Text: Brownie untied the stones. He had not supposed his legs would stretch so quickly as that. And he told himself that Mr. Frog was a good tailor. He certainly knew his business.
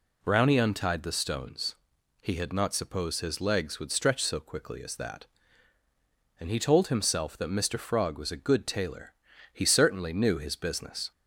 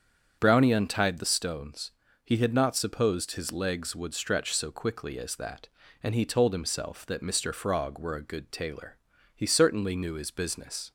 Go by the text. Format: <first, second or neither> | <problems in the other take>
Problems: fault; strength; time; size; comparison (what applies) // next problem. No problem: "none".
first | starts louder than the rest; strong; until 1.4 s; 7.5 dB // says "were" for "was"; at 7.9 s